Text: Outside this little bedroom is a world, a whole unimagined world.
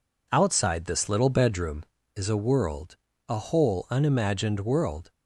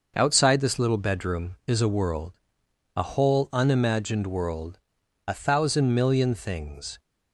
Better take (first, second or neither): first